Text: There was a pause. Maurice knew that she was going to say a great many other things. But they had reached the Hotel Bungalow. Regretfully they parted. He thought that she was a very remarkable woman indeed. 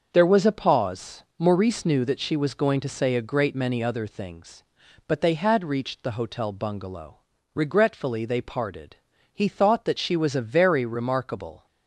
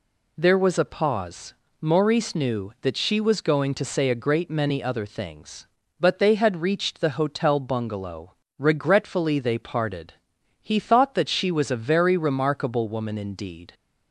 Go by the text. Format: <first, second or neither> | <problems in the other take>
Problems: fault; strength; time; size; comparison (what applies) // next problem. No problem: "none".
second | starts louder than the rest; until 1.1 s; 6.5 dB // stops before "woman indeed"; at 11.6 s